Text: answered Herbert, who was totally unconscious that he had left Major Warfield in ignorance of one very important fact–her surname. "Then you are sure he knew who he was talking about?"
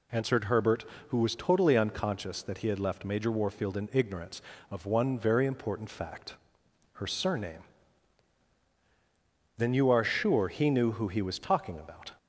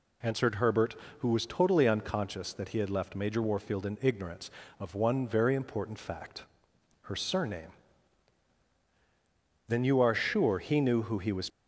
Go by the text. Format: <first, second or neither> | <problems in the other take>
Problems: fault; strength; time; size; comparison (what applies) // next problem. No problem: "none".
first | stops before "talking about"; at 11.4 s